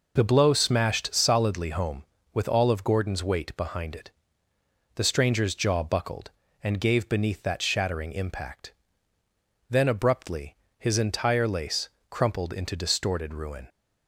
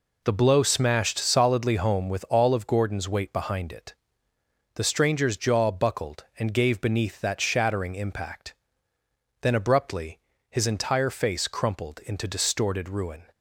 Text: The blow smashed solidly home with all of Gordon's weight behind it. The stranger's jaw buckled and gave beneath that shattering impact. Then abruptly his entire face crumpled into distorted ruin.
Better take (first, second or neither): second